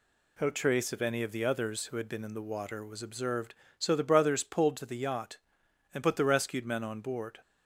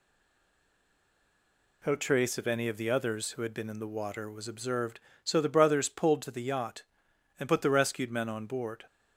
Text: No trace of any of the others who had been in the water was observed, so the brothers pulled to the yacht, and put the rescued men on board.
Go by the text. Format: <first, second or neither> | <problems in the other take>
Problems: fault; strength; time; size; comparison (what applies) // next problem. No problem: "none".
first | stays silent before the first word; noticeable; until 1.8 s; 1.8 s long